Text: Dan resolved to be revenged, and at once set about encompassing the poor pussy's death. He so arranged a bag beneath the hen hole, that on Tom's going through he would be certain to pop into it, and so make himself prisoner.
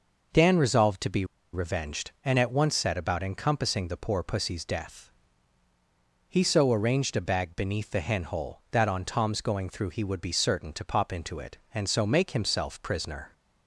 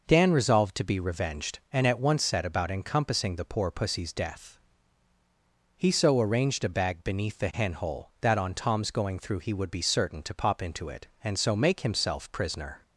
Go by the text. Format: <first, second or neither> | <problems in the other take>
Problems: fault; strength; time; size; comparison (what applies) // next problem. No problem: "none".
second | pauses between "be" and "revenged"; slight; at 1.2 s; 0.29 s long